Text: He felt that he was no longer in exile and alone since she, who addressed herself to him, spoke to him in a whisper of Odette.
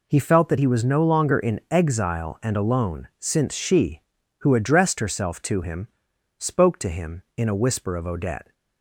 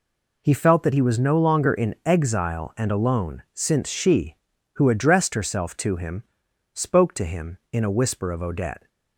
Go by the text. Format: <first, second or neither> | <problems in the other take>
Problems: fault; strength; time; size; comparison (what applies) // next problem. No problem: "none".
neither | none